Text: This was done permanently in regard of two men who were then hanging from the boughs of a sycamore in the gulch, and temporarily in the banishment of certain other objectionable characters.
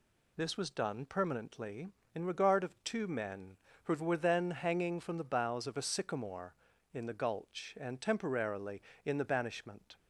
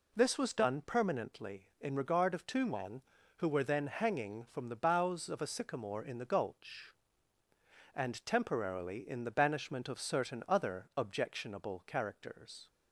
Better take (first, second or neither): second